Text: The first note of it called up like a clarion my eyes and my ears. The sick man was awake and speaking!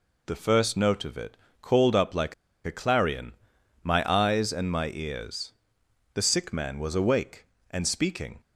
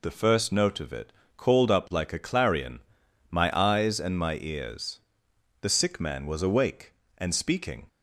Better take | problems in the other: second | pauses between "it" and "called"; slight; at 1.3 s; 0.24 s long; slight in the second // pauses between "like" and "a"; slight; at 2.3 s; 0.31 s long // pauses between "clarion" and "my"; noticeable; at 3.3 s; 0.50 s long; noticeable in the second

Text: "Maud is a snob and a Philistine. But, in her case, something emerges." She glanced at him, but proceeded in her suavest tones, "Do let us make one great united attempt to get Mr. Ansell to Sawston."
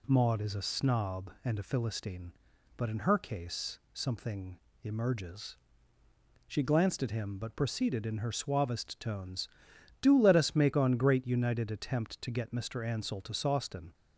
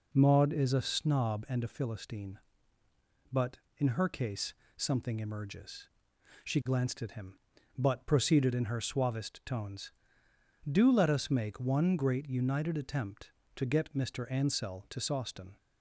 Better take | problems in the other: second | pauses between "something" and "emerges"; slight; at 4.5 s; 0.24 s long // says "on" for "one"; at 10.7 s

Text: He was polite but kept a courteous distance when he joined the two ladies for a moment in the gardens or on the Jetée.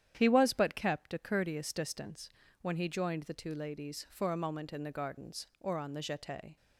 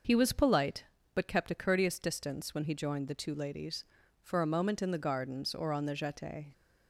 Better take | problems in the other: second | starts louder than the rest; strong; until 1.1 s; 10 dB; noticeable in the second // skips "polite"; at 0.5 s // pauses between "distance" and "when"; slight; at 2.2 s; 0.32 s long

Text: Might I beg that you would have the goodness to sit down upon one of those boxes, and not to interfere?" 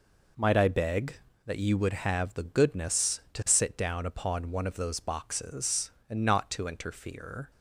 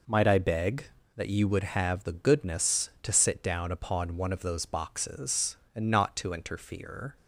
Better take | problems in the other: neither | none

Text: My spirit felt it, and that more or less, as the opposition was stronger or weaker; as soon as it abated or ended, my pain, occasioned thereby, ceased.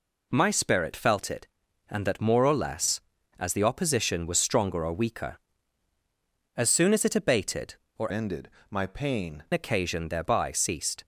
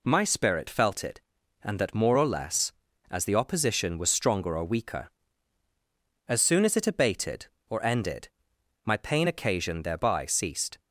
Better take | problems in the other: second | changes voice from "ended" to "pain"; from 8.1 to 9.4 s; 1.3 s long

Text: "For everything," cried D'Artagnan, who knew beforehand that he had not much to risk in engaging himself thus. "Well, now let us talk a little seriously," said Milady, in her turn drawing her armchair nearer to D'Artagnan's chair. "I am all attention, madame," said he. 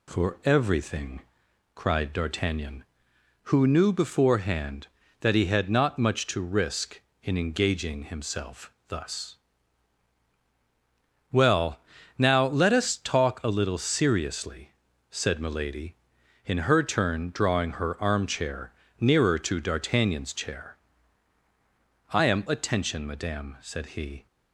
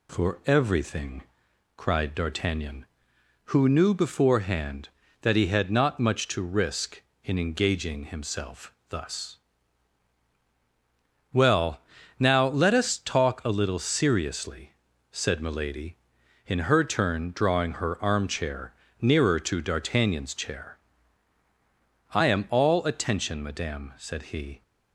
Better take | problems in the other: second | pauses between "armchair" and "nearer"; slight; at 18.7 s; 0.26 s long; slight in the second // skips "all"; at 22.4 s

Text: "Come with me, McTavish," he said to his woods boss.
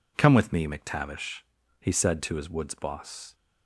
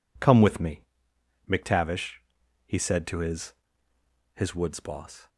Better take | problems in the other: first | says "his" twice; at 4.3 s

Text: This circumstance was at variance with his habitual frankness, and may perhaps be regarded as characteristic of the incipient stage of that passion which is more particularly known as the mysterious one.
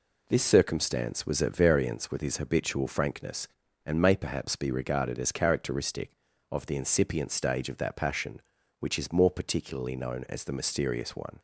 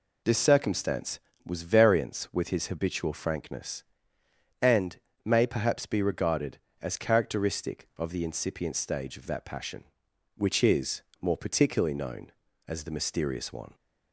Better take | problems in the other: first | skips "at"; at 1.6 s // pauses between "and" and "may"; slight; at 4.9 s; 0.26 s long // pauses between "is" and "more"; slight; at 11.0 s; 0.18 s long

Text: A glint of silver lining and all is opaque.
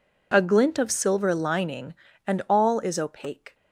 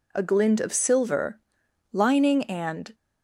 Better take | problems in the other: first | pauses between "silver" and "lining"; noticeable; at 1.3 s; 0.54 s long // stops before "all is opaque"; at 2.9 s

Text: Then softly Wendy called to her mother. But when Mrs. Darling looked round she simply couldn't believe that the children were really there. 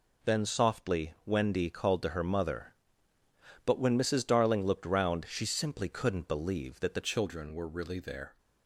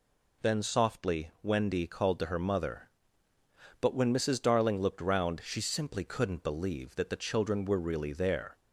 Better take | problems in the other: second | changes voice at "children"; from 7.0 s on; 1.3 s long

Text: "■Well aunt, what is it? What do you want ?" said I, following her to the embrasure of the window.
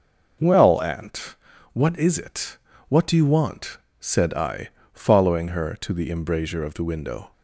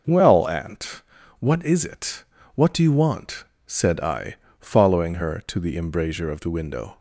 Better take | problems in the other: neither | none

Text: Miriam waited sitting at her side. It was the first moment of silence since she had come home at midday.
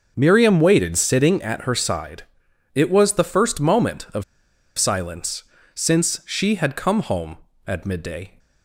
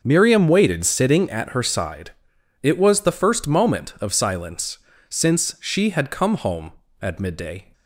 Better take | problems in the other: second | pauses between "of" and "silence"; noticeable; at 4.2 s; 0.54 s long // pauses between "silence" and "since"; slight; at 5.4 s; 0.32 s long; slight in the second

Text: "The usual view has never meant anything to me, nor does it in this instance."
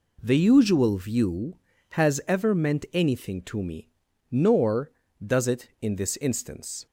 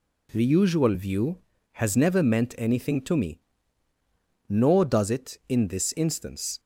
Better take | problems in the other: second | says "ever" for "never"; at 2.2 s

